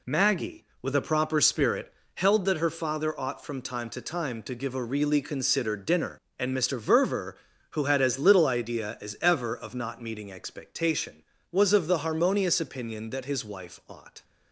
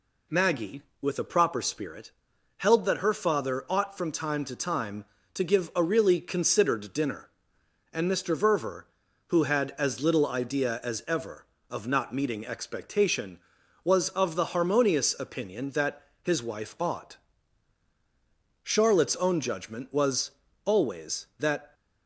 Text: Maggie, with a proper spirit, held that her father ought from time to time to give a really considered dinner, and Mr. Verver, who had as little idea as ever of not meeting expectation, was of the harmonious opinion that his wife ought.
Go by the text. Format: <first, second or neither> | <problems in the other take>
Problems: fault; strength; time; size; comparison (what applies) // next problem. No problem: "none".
first | pauses between "that" and "his"; slight; at 16.0 s; 0.18 s long // goes on to say "Charlotte's own judgment was always that"; strong; from 18.6 s on; 3.1 s long